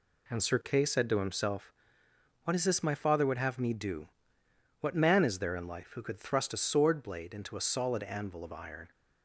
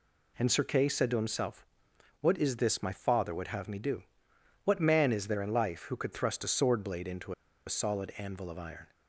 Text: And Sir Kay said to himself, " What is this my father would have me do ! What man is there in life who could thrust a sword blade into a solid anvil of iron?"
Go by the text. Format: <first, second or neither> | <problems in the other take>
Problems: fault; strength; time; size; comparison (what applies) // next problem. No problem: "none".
first | pauses between "into" and "a"; slight; at 7.3 s; 0.33 s long